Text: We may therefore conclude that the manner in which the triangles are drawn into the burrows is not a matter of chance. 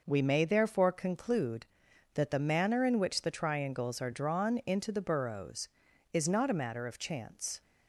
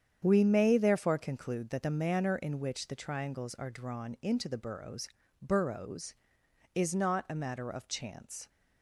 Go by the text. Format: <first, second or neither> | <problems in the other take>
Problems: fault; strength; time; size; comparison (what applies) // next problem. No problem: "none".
first | starts louder than the rest; strong; until 1.2 s; 8 dB // says "burrows" twice; at 5.4 s